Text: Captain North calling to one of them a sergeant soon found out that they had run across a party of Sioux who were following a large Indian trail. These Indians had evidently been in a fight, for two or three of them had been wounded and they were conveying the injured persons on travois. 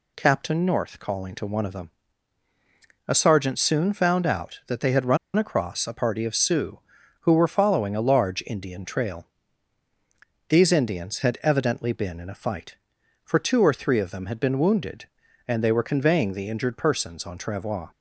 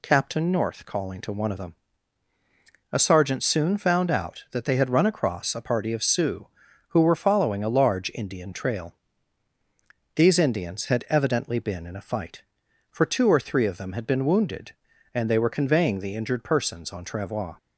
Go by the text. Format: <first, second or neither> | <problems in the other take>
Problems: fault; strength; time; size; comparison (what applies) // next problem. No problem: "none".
second | pauses between "them" and "a"; at 1.9 s; 1.1 s long; also in the second // pauses between "run" and "across"; slight; at 5.1 s; 0.19 s long